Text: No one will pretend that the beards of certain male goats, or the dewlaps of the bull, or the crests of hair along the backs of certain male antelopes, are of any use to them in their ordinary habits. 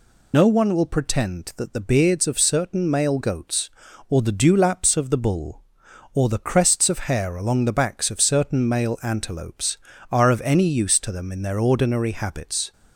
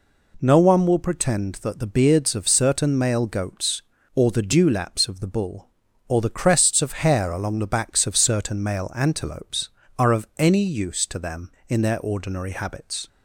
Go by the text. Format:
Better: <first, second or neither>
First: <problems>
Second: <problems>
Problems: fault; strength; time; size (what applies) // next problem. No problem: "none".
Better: second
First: loses the start of "No"; at 0.3 s; 75 ms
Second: none